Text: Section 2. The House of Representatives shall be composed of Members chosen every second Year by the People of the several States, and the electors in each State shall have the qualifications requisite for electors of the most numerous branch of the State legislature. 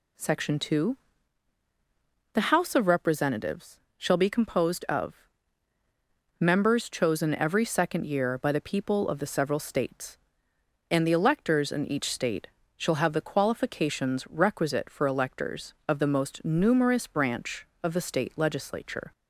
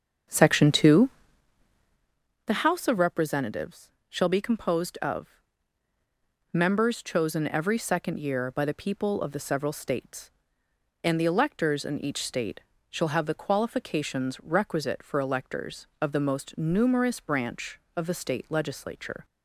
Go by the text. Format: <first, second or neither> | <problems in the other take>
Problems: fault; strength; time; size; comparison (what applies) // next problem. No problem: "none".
first | starts louder than the rest; strong; until 2.1 s; 7.5 dB // pauses between "Representatives" and "shall"; slight; at 3.9 s; 0.16 s long; slight in the first // pauses between "of" and "Members"; at 5.2 s; 1.2 s long; also in the first // pauses between "State" and "shall"; slight; at 12.5 s; 0.32 s long; slight in the first